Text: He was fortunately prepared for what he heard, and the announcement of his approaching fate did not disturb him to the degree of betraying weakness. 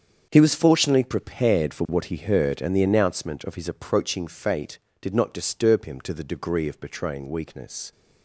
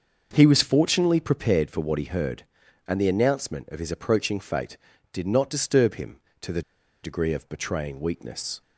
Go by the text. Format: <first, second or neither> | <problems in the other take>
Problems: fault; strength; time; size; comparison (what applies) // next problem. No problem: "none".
first | starts louder than the rest; until 1.3 s; 6.5 dB; strong in the first // pauses between "the" and "degree"; at 6.6 s; 0.41 s long